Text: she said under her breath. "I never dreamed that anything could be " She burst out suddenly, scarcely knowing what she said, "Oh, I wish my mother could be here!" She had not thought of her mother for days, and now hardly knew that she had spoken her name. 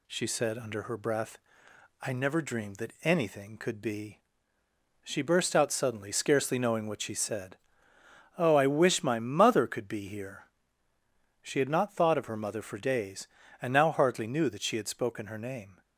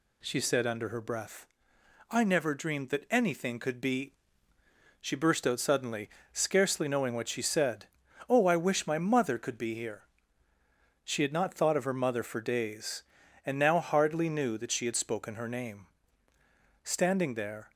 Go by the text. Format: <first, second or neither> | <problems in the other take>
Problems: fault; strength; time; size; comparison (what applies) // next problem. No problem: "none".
first | goes on to say "Standing there"; noticeable; from 16.8 s on; 0.88 s long